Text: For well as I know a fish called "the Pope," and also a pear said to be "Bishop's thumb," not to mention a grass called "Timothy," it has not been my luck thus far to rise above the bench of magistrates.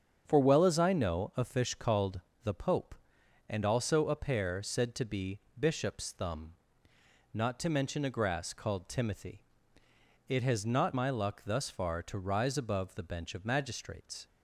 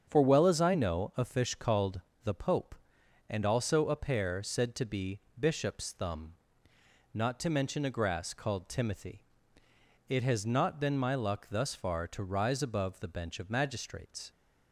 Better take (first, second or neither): second